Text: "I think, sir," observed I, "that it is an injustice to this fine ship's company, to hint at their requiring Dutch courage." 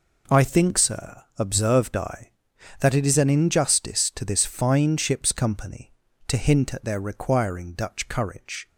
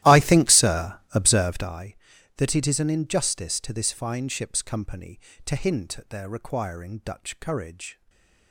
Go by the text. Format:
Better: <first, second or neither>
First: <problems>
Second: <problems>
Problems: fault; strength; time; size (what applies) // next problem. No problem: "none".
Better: first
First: none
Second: starts louder than the rest; strong; until 1.8 s; 15 dB // stays silent after the last word; slight; from 7.9 s on; 0.6 s long